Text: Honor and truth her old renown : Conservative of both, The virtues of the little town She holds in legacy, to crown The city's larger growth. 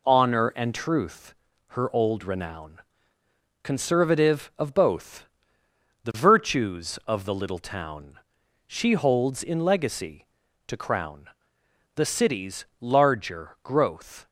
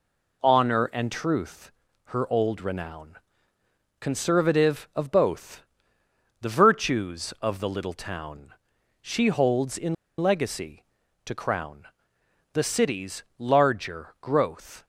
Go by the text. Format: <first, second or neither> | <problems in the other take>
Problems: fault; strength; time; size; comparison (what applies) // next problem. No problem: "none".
first | pauses between "truth" and "her"; at 1.7 s; 0.40 s long; also in the first // pauses between "town" and "She"; noticeable; at 8.5 s; 0.48 s long; noticeable in the first // pauses between "in" and "legacy"; slight; at 9.9 s; 0.25 s long // pauses between "crown" and "The"; noticeable; at 11.8 s; 0.66 s long; noticeable in the first // pauses between "city's" and "larger"; slight; at 13.2 s; 0.16 s long; slight in the first